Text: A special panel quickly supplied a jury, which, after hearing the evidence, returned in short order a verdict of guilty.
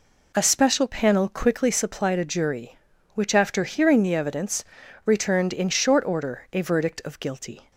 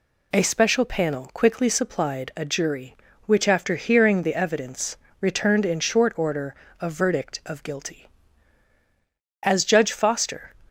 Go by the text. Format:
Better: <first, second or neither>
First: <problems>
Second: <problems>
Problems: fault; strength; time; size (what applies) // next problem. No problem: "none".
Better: first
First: none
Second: pauses between "order" and "a"; slight; at 6.5 s; 0.26 s long // goes on to say "As Judge Foster"; noticeable; from 9.4 s on; 1.1 s long